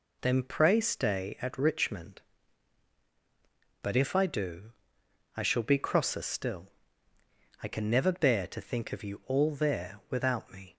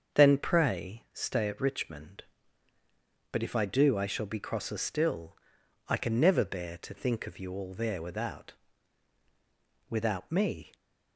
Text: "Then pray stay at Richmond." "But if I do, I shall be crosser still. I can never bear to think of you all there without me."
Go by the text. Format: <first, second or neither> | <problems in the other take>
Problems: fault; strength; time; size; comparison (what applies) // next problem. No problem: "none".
first | starts louder than the rest; until 1.2 s; 6.5 dB // says "without" twice; at 9.8 s